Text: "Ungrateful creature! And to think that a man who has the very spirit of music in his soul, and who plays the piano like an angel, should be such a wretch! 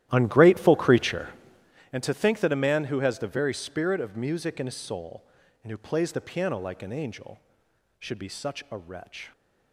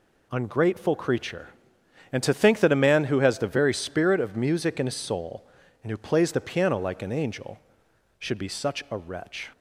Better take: second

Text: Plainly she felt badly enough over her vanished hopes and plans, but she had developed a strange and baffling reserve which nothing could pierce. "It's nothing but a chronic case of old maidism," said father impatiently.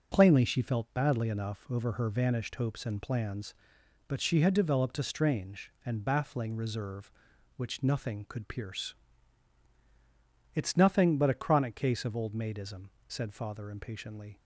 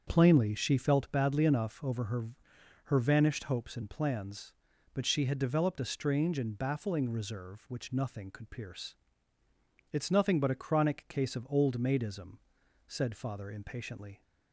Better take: first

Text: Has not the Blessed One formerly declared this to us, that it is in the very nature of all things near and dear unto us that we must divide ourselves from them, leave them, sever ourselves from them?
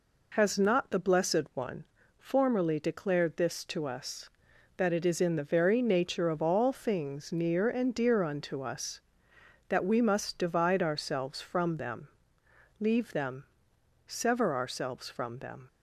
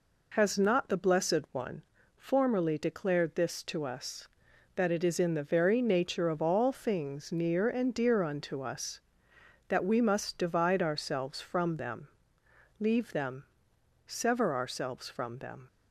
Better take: neither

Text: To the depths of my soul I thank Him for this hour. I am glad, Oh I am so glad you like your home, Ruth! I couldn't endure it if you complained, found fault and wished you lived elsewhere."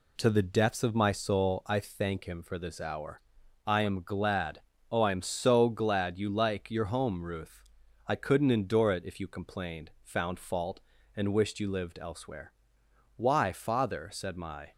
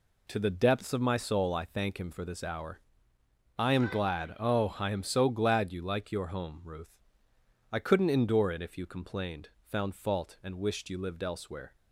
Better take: second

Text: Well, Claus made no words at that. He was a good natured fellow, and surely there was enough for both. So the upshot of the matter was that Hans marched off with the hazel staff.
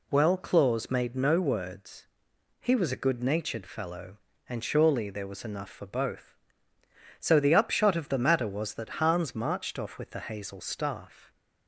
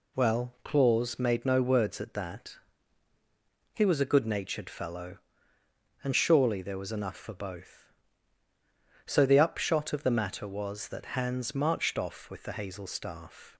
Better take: second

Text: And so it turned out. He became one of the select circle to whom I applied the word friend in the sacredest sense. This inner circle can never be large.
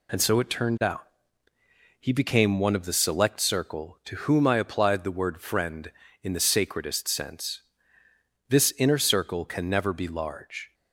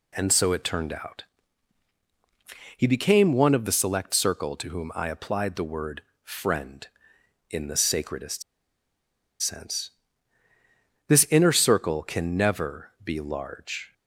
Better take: first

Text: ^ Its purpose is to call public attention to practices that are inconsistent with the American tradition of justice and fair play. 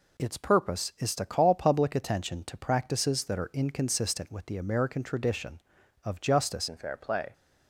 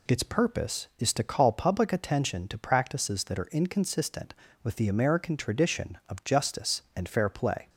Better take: second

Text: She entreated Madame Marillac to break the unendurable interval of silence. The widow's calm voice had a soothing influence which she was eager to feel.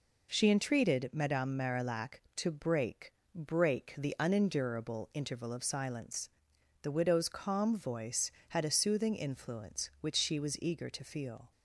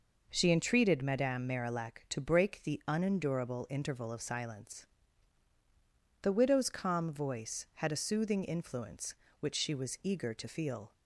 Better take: second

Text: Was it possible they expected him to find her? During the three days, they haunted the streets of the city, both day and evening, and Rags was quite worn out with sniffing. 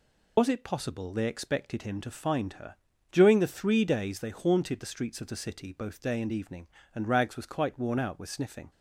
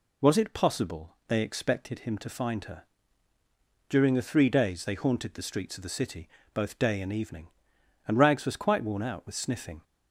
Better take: second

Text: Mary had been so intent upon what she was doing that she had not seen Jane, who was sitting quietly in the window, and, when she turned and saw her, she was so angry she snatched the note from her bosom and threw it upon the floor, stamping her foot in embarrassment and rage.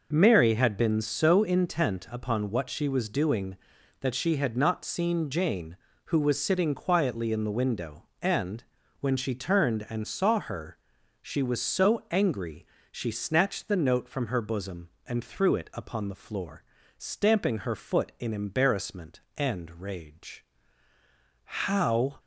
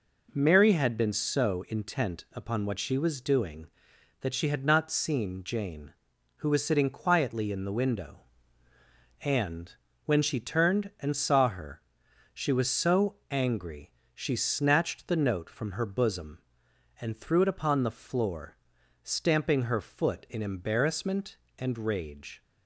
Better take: second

